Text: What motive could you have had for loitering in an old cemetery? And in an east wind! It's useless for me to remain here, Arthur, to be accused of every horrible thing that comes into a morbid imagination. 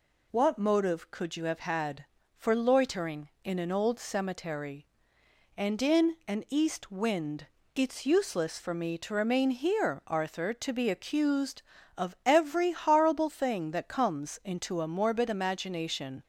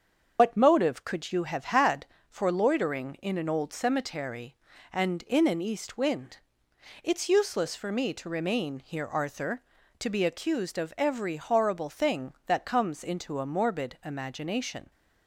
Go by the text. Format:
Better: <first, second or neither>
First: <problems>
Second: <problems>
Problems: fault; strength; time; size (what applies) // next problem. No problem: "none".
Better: first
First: none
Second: loses the start of "What"; at 0.3 s; 95 ms // starts louder than the rest; until 1.4 s; 7 dB